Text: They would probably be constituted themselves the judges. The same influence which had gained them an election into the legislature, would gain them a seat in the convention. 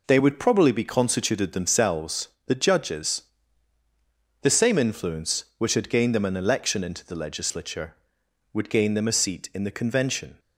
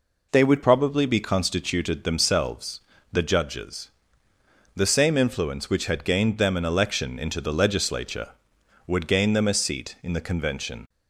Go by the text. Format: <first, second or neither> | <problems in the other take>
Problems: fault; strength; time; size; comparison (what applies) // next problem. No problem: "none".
first | changes voice at "probably"; from 0.6 s on; 10.2 s long // pauses between "themselves" and "the"; slight; at 2.8 s; 0.30 s long; slight in the first